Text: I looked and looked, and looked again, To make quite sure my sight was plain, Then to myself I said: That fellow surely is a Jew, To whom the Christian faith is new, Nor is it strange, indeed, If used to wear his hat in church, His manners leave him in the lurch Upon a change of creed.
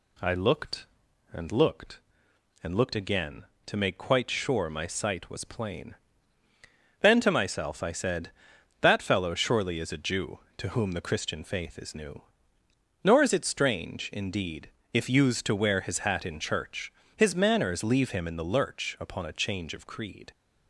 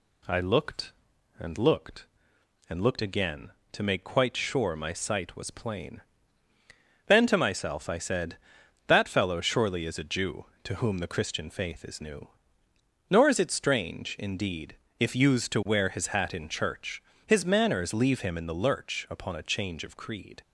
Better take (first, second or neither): neither